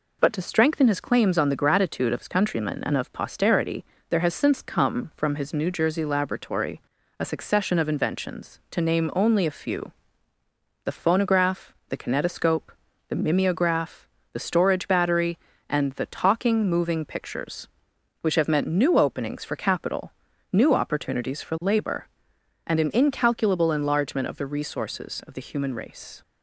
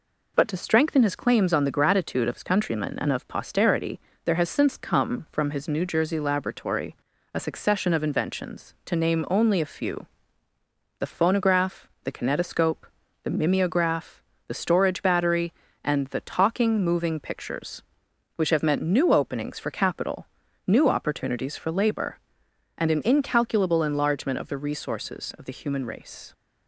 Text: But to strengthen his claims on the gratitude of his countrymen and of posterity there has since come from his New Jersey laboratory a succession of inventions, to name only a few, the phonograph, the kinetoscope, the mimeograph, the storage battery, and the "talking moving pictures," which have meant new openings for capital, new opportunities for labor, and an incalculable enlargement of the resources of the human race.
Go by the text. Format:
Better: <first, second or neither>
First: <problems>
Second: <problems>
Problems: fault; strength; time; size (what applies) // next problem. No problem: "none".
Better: neither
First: pauses between "posterity" and "there"; slight; at 3.8 s; 0.26 s long // pauses between "laboratory" and "a"; slight; at 6.8 s; 0.36 s long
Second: pauses between "posterity" and "there"; slight; at 3.9 s; 0.26 s long // pauses between "laboratory" and "a"; slight; at 6.9 s; 0.36 s long